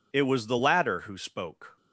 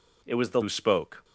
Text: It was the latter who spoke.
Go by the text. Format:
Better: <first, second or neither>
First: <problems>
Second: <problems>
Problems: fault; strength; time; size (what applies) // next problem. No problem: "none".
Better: first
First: none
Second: skips "latter"; at 0.6 s